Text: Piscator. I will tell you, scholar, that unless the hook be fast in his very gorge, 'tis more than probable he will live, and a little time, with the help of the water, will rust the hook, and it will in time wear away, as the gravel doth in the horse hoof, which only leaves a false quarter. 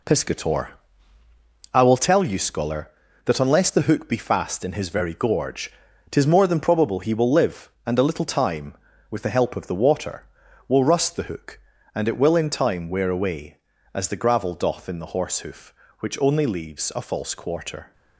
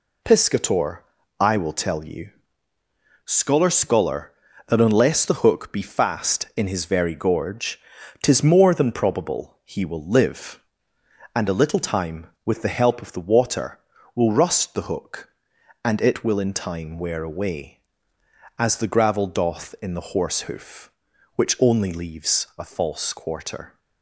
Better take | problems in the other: first | says "scholar" twice; at 3.7 s

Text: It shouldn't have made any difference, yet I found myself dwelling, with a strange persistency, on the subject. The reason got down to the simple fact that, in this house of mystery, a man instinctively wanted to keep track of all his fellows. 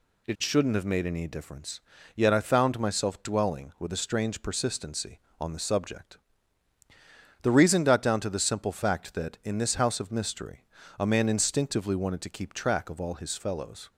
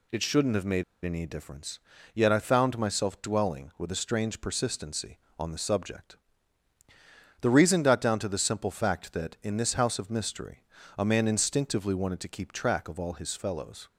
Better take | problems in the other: first | pauses between "made" and "any"; slight; at 0.8 s; 0.21 s long

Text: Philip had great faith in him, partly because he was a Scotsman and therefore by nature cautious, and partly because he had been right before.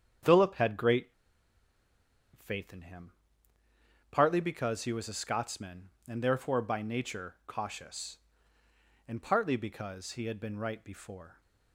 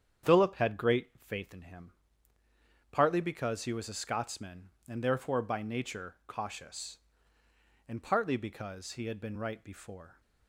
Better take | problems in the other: second | starts louder than the rest; strong; until 2.5 s; 8.5 dB; strong in the second // pauses between "great" and "faith"; strong; at 1.0 s; 1.2 s long

